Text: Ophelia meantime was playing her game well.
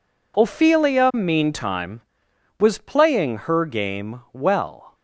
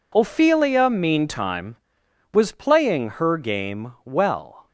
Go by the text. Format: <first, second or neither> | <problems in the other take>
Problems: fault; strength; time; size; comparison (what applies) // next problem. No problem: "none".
neither | none